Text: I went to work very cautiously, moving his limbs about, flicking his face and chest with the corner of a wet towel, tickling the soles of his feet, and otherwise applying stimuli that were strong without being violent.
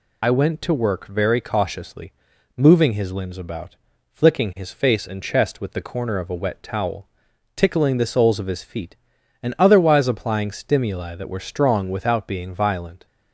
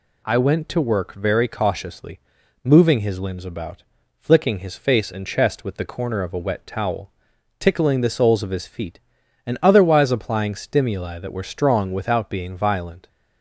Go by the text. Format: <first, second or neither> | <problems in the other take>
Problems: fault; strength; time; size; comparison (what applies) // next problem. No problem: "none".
second | loses the start of "I"; at 0.2 s; 50 ms